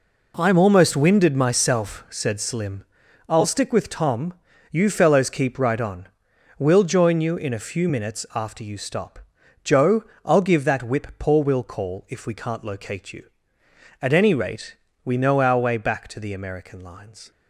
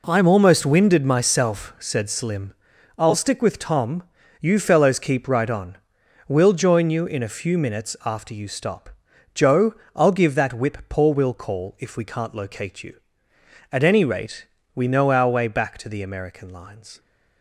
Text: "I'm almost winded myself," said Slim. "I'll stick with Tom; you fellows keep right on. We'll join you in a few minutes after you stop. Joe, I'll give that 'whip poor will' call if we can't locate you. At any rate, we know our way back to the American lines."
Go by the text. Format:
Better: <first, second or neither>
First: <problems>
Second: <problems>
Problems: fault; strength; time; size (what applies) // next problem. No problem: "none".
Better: neither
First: none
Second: none